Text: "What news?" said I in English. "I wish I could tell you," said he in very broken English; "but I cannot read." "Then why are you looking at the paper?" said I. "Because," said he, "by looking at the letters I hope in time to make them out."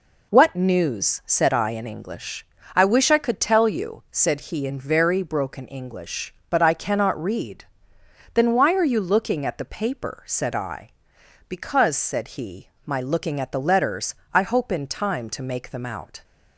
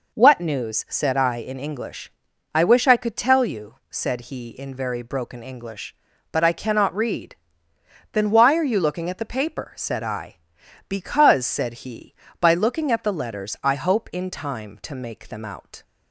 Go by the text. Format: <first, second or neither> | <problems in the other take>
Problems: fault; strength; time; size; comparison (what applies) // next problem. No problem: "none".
second | says "my" for "by"; at 12.8 s // pauses between "letters" and "I"; slight; at 14.1 s; 0.18 s long